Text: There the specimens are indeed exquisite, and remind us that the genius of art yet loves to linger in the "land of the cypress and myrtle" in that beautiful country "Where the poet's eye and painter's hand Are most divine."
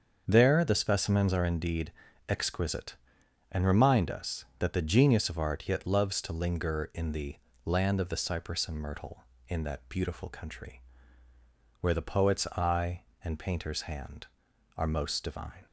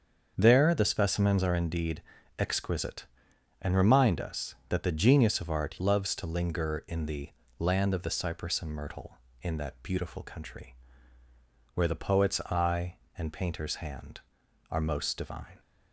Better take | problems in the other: first | starts louder than the rest; until 1.3 s; 7 dB; also in the first // pauses between "indeed" and "exquisite"; slight; at 2.0 s; 0.36 s long; slight in the first // skips "yet"; at 5.7 s // pauses between "the" and "land"; slight; at 7.2 s; 0.30 s long; slight in the first // pauses between "country" and "Where"; at 10.7 s; 1.0 s long; also in the first

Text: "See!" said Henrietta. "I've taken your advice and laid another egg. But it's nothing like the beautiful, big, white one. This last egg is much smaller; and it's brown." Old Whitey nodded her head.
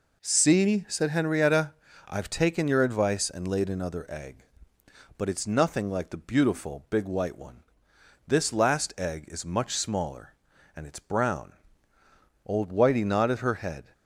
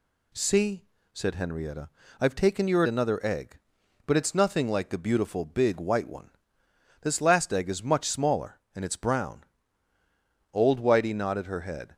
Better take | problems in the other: first | skips "advice and laid"; at 2.8 s

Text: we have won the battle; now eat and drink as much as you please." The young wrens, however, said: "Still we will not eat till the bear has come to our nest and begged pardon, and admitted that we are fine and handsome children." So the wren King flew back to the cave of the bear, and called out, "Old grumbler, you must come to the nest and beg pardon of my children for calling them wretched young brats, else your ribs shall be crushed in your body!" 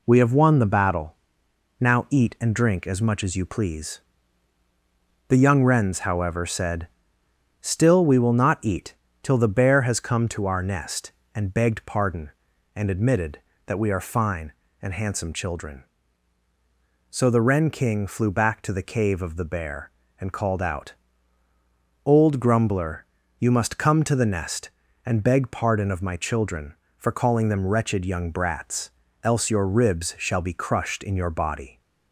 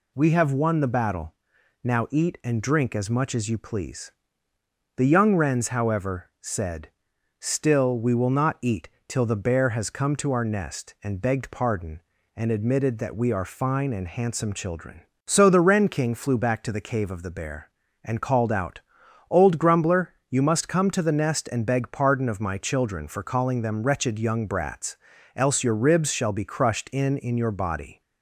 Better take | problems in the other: first | pauses between "eat" and "till"; slight; at 8.8 s; 0.18 s long; slight in the first // says "in" twice; at 27.1 s

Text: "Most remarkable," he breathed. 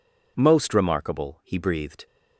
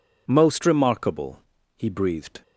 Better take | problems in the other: first | changes voice at "remarkable"; from 0.6 s on; 1.8 s long

